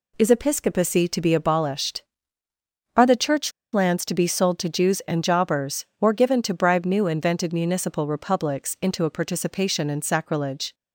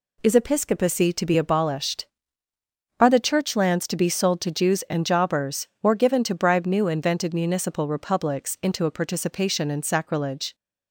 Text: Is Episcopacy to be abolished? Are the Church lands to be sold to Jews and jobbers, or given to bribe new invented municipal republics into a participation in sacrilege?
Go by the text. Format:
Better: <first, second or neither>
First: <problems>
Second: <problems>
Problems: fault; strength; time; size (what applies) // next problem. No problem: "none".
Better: second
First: pauses between "Church" and "lands"; slight; at 3.5 s; 0.22 s long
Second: none